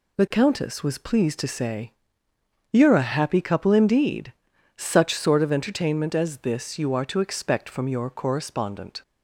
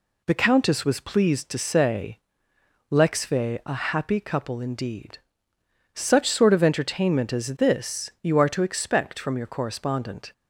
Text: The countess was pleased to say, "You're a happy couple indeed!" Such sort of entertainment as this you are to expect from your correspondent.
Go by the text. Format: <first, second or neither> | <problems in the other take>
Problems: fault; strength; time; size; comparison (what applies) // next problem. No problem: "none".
first | says "Lexve" for "You're"; at 2.8 s